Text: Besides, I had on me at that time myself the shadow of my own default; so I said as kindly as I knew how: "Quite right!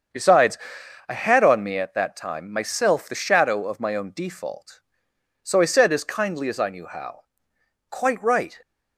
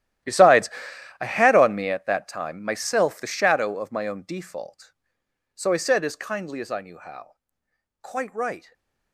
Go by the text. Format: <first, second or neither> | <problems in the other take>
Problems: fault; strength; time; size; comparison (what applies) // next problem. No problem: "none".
first | gets quieter; strong; throughout; 17 dB // starts louder than the rest; strong; until 1.7 s; 13 dB; strong in the first // stays silent after the last word; slight; from 8.5 s on; 0.6 s long